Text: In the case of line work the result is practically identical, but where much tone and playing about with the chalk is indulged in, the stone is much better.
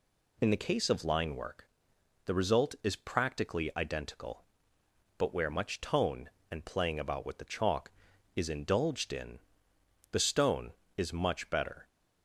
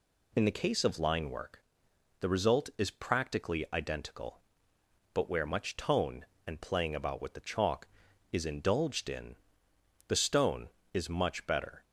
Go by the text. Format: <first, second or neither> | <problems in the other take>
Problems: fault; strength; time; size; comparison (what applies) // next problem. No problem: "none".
neither | pauses between "work" and "the"; noticeable; the same in both